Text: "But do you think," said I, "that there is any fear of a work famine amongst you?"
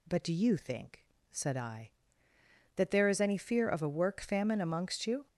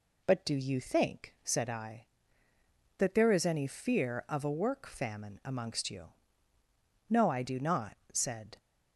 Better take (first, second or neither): first